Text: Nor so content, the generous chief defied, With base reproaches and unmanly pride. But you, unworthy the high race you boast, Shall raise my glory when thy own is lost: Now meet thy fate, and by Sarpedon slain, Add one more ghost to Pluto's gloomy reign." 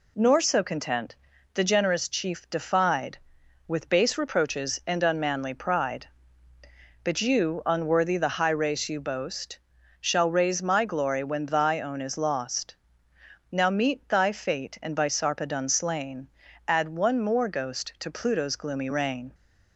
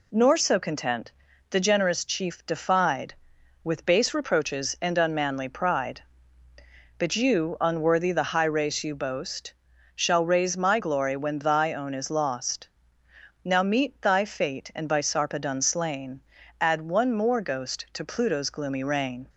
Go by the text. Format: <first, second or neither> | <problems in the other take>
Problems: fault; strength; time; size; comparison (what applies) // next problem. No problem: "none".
neither | none